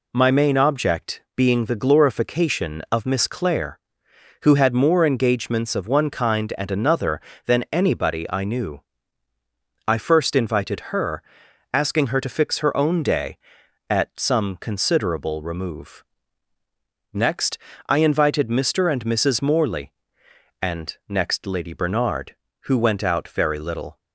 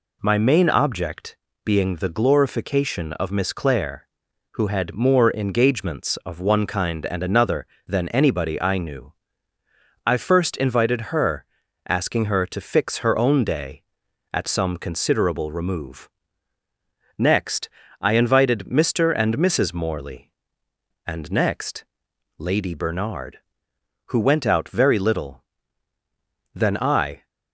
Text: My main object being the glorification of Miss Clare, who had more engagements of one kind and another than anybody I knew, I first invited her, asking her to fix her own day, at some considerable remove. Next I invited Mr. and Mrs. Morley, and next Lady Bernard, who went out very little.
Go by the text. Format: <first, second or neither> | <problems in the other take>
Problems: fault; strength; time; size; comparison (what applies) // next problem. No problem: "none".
first | pauses between "object" and "being"; slight; at 1.3 s; 0.26 s long // pauses between "Next" and "I"; slight; at 17.6 s; 0.32 s long; slight in the first // pauses between "next" and "Lady"; noticeable; at 21.8 s; 0.52 s long // goes on to say "Then I"; noticeable; from 26.5 s on; 0.74 s long